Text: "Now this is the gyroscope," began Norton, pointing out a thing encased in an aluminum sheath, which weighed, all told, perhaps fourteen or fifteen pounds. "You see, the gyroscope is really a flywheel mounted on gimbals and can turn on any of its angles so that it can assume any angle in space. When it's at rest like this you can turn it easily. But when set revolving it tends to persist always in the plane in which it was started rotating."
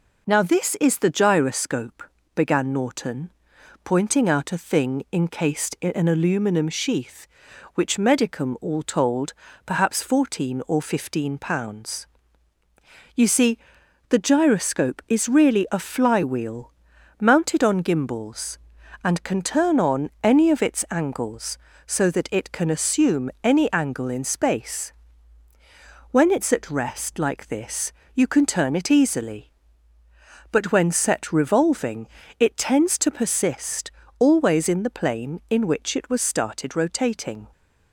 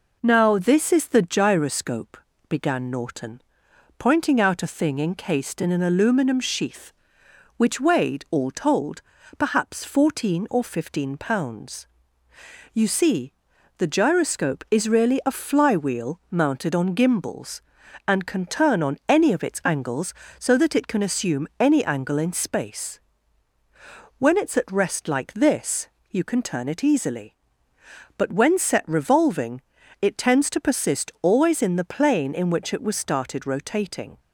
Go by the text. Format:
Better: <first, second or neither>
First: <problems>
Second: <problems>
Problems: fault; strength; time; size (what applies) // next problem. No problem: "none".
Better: second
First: says "medicum" for "weighed"; at 7.9 s // pauses between "flywheel" and "mounted"; noticeable; at 16.7 s; 0.50 s long // pauses between "this" and "you"; slight; at 27.9 s; 0.22 s long // pauses between "revolving" and "it"; slight; at 32.0 s; 0.32 s long // pauses between "persist" and "always"; slight; at 33.9 s; 0.28 s long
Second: pauses between "this" and "you"; slight; at 25.8 s; 0.22 s long // pauses between "revolving" and "it"; at 29.6 s; 0.40 s long